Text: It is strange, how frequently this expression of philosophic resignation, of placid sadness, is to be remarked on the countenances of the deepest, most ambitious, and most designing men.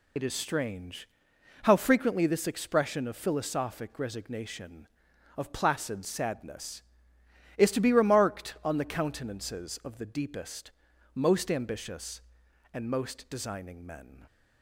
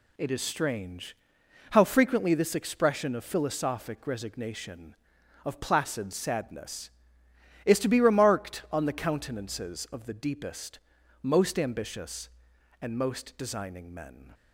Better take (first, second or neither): second